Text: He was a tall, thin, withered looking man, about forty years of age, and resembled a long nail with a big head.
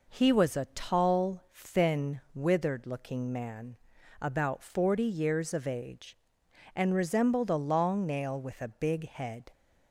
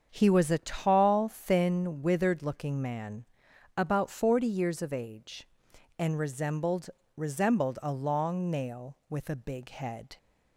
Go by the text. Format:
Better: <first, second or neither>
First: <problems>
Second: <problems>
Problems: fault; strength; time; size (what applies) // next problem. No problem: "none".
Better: first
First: none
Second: starts louder than the rest; until 1.1 s; 7 dB // says "resembled" twice; at 7.1 s